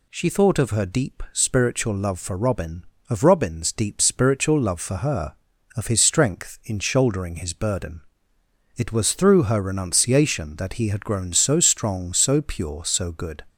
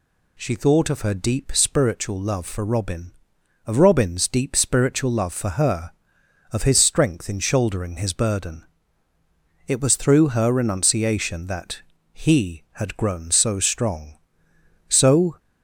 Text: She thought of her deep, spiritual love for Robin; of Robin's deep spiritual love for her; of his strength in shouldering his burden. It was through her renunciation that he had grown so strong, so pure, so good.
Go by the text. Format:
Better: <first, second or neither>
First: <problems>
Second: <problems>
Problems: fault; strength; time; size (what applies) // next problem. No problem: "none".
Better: first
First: none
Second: pauses between "that" and "he"; slight; at 11.8 s; 0.30 s long // stops before "pure so good"; at 15.3 s